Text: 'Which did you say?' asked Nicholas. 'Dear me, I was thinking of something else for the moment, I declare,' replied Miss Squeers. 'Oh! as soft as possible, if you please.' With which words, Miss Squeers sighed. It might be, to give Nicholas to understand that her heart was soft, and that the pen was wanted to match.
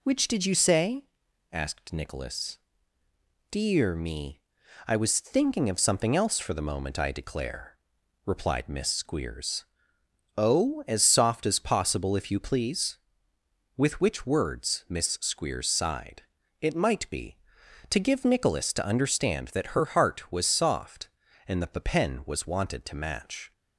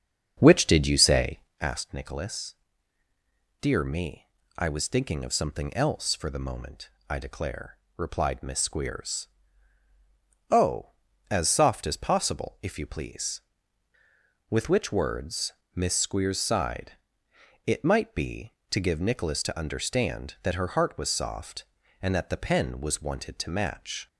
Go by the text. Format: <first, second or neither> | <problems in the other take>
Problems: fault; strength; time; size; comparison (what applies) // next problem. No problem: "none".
first | starts louder than the rest; strong; until 1.7 s; 7.5 dB